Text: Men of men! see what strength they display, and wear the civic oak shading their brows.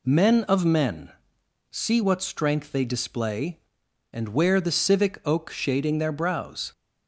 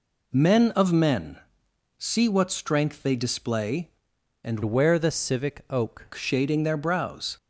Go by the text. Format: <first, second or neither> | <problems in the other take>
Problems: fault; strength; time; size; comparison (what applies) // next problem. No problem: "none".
first | changes voice from "wear" to "oak"; from 4.6 to 6.0 s; 1.4 s long